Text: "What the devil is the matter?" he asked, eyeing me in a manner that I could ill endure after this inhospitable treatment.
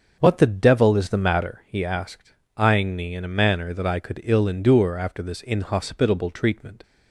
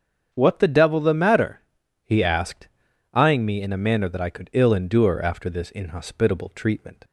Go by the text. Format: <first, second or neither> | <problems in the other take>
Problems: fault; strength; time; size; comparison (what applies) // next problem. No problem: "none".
first | starts louder than the rest; strong; until 1.3 s; 7.5 dB; also in the first // skips "is"; at 0.9 s